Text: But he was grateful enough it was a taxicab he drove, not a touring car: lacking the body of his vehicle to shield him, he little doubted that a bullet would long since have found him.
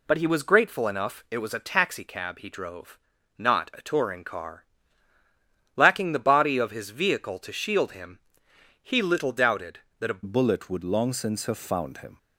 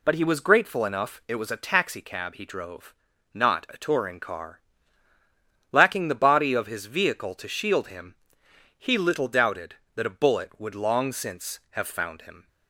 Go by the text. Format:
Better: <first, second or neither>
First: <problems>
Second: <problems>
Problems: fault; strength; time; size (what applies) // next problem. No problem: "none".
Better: second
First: changes voice at "bullet"; from 10.2 s on; 1.9 s long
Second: none